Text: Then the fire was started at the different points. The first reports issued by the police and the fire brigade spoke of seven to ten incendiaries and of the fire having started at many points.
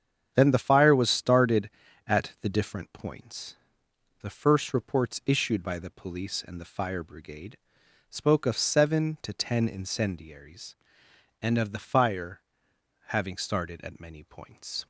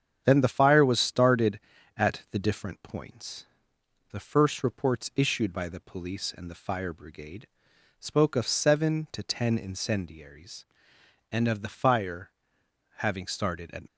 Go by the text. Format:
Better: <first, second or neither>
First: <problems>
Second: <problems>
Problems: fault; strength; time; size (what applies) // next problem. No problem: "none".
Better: first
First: starts louder than the rest; strong; until 1.3 s; 8 dB // pauses between "brigade" and "spoke"; noticeable; at 7.5 s; 0.52 s long // pauses between "fire" and "having"; noticeable; at 12.4 s; 0.68 s long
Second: starts louder than the rest; strong; until 1.2 s; 8 dB // pauses between "brigade" and "spoke"; noticeable; at 7.4 s; 0.52 s long // pauses between "fire" and "having"; noticeable; at 12.3 s; 0.68 s long // stops before "many points"; at 13.8 s